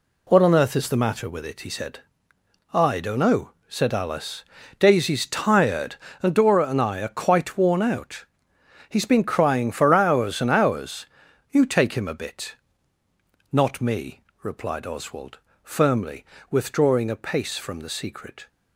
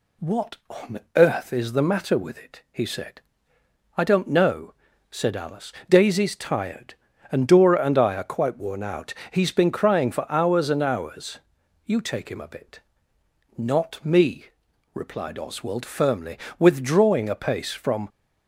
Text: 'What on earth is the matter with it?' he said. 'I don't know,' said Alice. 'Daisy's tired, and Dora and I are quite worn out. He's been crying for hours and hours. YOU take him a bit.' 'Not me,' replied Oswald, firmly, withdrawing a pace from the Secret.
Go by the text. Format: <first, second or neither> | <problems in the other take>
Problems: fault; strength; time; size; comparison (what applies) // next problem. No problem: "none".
first | pauses between "on" and "earth"; slight; at 0.9 s; 0.16 s long // stops before "the Secret"; at 18.0 s